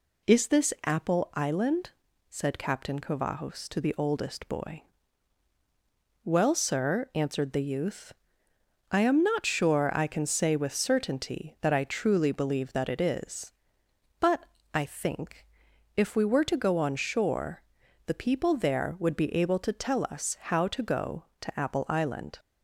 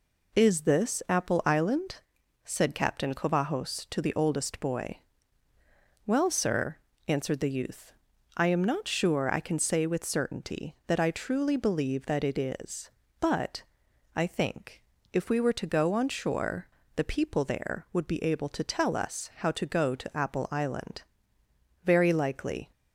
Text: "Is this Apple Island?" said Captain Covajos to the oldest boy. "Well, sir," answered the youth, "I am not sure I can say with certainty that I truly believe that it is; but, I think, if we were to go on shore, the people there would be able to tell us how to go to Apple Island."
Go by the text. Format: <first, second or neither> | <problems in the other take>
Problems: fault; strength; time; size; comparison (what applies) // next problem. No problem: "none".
first | goes on to say "Very likely"; noticeable; from 21.8 s on; 0.88 s long